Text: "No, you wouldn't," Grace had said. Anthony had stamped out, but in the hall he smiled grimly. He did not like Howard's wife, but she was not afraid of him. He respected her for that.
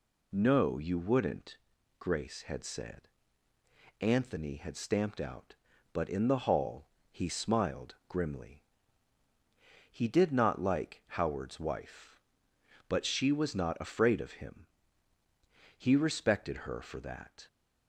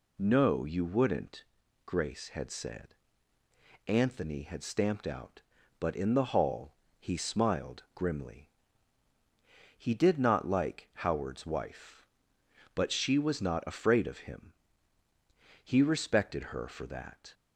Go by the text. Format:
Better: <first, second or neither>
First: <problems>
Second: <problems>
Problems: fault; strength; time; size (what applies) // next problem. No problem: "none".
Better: neither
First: pauses between "hall" and "he"; slight; at 6.8 s; 0.24 s long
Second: pauses between "hall" and "he"; slight; at 6.7 s; 0.26 s long